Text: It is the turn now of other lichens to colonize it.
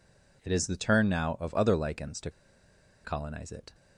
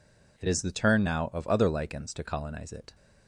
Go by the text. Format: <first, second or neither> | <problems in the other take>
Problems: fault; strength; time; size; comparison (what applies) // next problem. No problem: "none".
second | pauses between "to" and "colonize"; noticeable; at 2.2 s; 0.74 s long